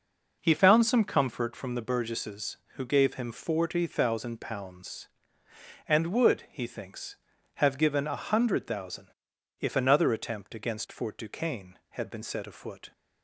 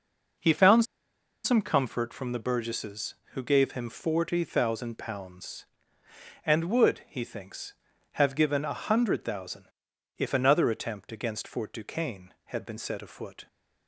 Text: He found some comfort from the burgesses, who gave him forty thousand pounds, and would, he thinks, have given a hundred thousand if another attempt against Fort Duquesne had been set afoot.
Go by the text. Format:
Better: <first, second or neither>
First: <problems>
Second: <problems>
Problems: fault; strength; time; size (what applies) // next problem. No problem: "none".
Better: first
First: pauses between "thousand" and "if"; noticeable; at 9.0 s; 0.50 s long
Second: pauses between "found" and "some"; noticeable; at 0.8 s; 0.60 s long // pauses between "thousand" and "if"; noticeable; at 9.6 s; 0.50 s long